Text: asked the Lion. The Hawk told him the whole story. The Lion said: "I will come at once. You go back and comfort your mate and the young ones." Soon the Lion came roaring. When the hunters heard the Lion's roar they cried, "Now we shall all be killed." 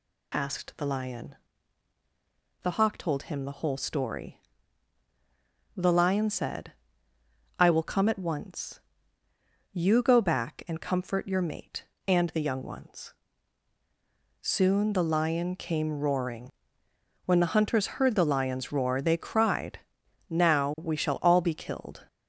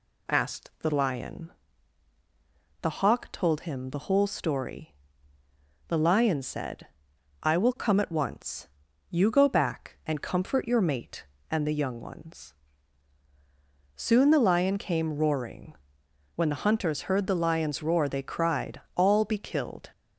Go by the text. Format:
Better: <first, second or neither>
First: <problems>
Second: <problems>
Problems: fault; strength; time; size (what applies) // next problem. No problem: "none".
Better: first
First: none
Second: skips "Now we shall"; at 18.8 s